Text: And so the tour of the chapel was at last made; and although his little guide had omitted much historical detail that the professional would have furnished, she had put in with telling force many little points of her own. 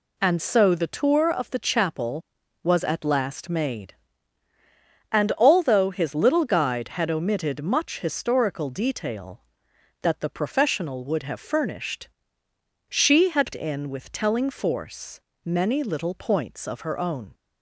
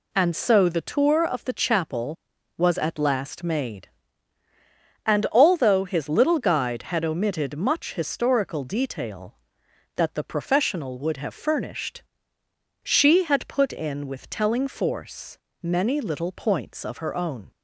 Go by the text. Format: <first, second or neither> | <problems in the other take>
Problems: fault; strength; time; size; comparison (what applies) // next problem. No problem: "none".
second | skips "put"; at 13.5 s // pauses between "force" and "many"; slight; at 15.1 s; 0.26 s long; slight in the second